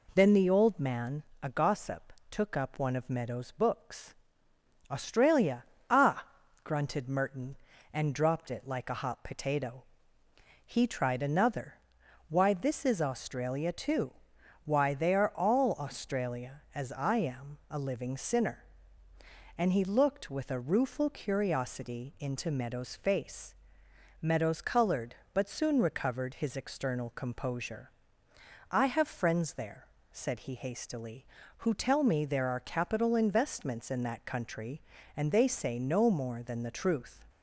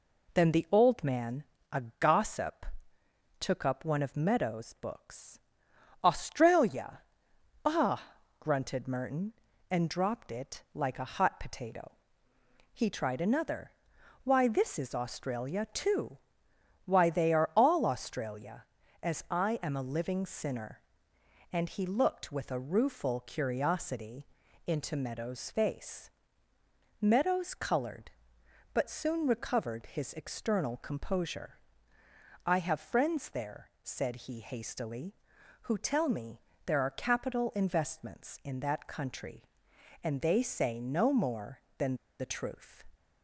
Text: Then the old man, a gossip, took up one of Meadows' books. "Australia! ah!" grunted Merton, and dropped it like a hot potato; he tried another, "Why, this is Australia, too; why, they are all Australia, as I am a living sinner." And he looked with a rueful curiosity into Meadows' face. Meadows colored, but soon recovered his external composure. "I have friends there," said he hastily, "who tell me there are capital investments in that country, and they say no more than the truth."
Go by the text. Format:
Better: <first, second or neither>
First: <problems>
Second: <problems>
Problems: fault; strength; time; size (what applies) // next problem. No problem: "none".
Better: first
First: none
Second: pauses between "a" and "gossip"; slight; at 1.8 s; 0.18 s long // pauses between "curiosity" and "into"; at 24.2 s; 0.38 s long // pauses between "me" and "there"; slight; at 36.3 s; 0.26 s long // pauses between "than" and "the"; slight; at 41.9 s; 0.24 s long